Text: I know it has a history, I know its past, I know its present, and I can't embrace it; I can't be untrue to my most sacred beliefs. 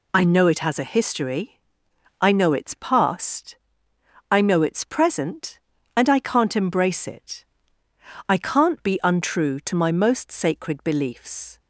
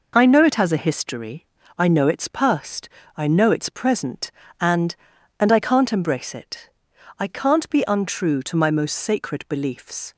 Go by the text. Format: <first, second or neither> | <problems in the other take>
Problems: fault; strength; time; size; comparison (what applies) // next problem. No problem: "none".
first | says "and" twice; at 5.4 s